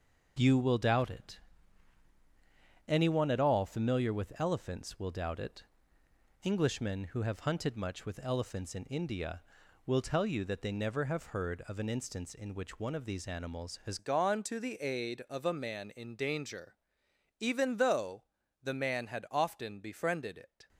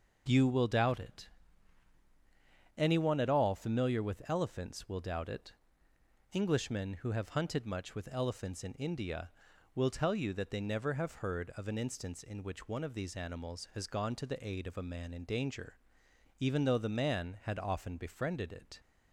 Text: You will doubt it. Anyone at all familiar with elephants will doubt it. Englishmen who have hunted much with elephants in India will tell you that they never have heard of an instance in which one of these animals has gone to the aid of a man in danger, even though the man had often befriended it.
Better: second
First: changes voice at "gone"; from 13.9 s on; 6.7 s long // pauses between "though" and "the"; at 18.2 s; 0.38 s long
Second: none

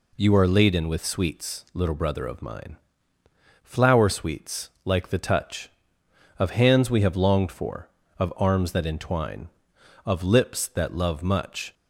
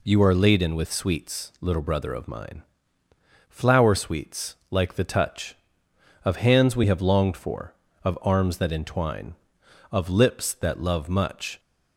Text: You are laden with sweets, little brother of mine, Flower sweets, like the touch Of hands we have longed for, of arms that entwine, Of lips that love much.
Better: neither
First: none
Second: none

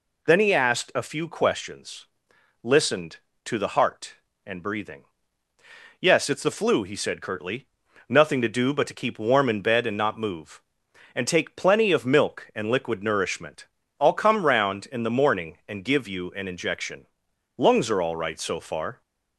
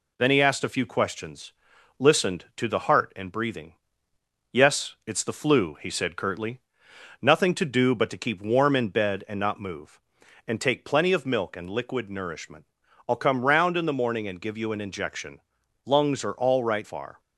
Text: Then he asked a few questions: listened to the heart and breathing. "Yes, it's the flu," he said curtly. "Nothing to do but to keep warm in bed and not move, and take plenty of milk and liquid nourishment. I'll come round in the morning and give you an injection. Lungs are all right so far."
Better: first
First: none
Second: skips "so"; at 16.8 s

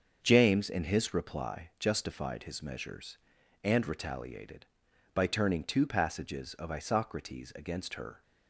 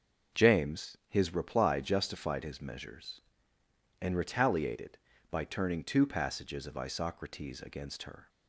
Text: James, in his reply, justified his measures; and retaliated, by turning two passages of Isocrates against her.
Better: first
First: starts louder than the rest; until 1.2 s; 7 dB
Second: starts louder than the rest; noticeable; until 1.4 s; 6 dB // skips "in"; at 1.0 s

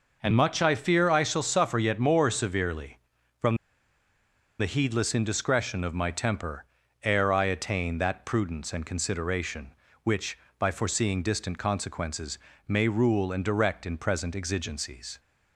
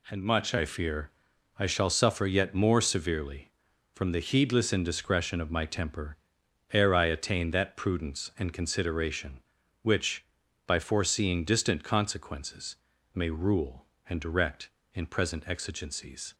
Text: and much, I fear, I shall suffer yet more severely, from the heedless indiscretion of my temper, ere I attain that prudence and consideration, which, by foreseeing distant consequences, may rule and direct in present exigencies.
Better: second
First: pauses between "from" and "the"; at 3.5 s; 1.0 s long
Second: none

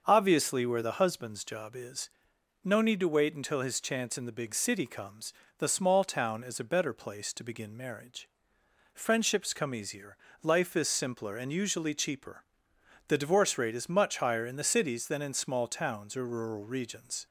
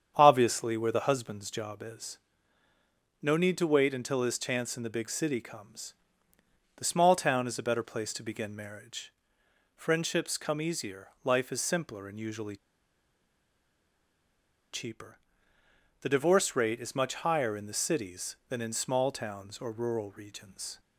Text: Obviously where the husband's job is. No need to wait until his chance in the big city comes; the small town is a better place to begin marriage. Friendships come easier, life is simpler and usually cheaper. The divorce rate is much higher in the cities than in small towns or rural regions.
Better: first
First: starts louder than the rest; until 1.0 s; 6.5 dB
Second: starts louder than the rest; strong; until 1.1 s; 8 dB // pauses between "usually" and "cheaper"; strong; at 12.5 s; 2.1 s long

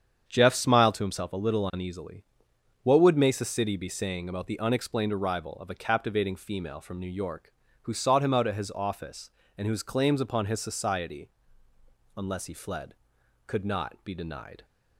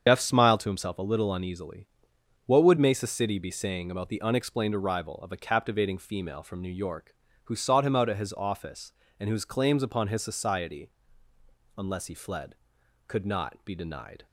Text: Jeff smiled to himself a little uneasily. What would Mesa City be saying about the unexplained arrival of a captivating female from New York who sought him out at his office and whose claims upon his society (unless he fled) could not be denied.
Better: first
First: starts louder than the rest; strong; until 1.3 s; 7.5 dB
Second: loses the start of "Jeff"; at 0.0 s; 130 ms // starts louder than the rest; strong; until 1.0 s; 7.5 dB

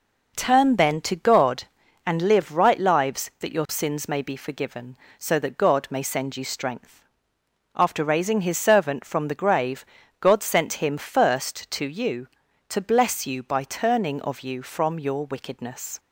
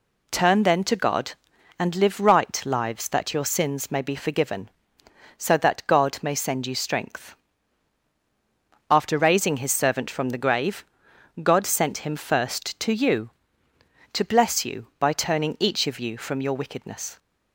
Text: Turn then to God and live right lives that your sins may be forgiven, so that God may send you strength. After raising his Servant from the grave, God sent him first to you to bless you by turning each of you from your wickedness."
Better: second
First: skips "each"; at 14.2 s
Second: none

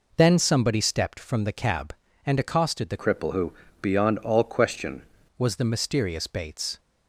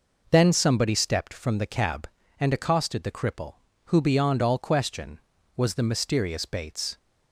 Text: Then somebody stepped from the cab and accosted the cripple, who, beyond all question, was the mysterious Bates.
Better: second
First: changes voice from "cripple" to "question"; from 2.9 to 5.0 s; 2.1 s long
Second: none

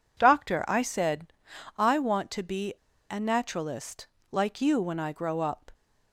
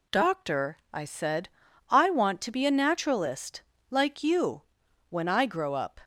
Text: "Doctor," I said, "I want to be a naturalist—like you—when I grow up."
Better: second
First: pauses between "be" and "a"; at 2.7 s; 0.36 s long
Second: none

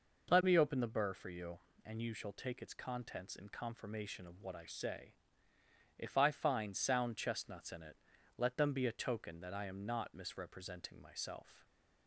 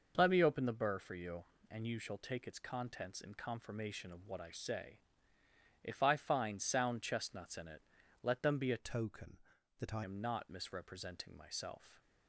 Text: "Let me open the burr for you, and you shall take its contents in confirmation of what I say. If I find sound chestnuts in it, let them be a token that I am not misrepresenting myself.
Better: first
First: none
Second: changes voice from "token" to "I"; from 8.7 to 10.0 s; 1.3 s long

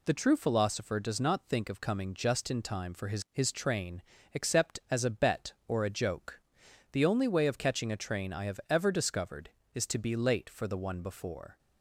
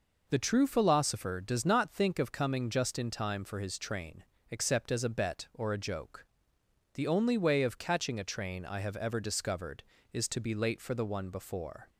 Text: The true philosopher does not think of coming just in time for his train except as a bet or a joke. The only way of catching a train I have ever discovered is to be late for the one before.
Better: second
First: says "his" twice; at 3.3 s // pauses between "train" and "except"; slight; at 4.0 s; 0.30 s long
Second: pauses between "train" and "except"; slight; at 4.2 s; 0.26 s long

